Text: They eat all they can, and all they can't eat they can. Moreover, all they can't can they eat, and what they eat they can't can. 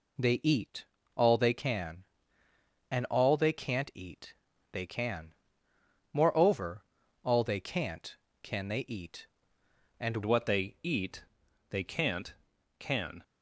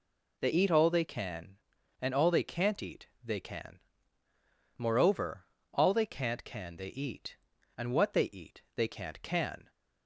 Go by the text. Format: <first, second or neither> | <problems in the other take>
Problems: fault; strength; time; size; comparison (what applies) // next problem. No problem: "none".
second | pauses between "eat" and "all"; slight; at 0.8 s; 0.30 s long // pauses between "eat" and "they"; at 4.3 s; 0.38 s long; slight in the second // changes voice at "what"; from 10.2 s on; 3.0 s long // pauses between "eat" and "they"; noticeable; at 11.2 s; 0.46 s long; slight in the second